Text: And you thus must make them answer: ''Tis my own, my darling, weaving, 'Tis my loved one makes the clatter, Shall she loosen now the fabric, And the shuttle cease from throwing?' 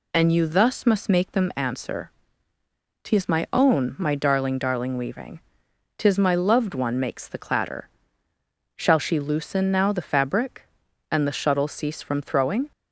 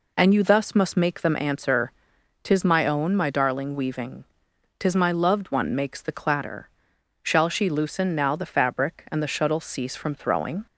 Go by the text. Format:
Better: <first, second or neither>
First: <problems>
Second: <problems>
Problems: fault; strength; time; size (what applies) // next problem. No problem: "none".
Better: second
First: says "darling" twice; at 4.5 s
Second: none